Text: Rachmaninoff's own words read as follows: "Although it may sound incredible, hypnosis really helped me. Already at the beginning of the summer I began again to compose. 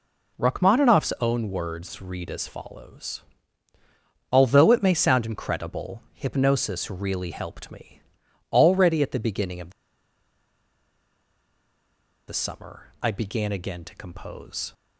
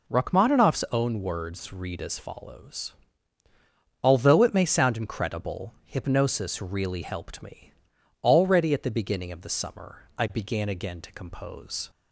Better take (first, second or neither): second